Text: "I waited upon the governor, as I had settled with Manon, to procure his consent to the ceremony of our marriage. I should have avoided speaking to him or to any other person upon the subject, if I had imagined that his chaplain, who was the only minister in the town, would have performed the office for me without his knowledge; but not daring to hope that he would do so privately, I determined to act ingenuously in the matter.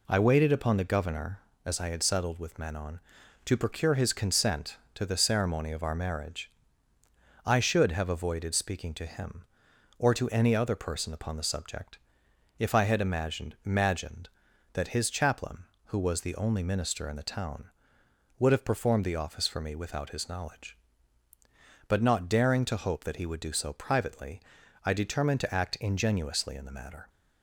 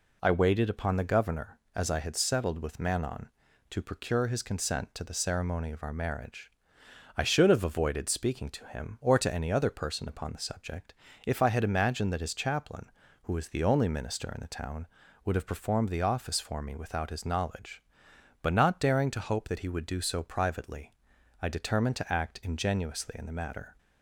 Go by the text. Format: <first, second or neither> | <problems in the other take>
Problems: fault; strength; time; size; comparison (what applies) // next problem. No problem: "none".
second | says "imagined" twice; at 13.6 s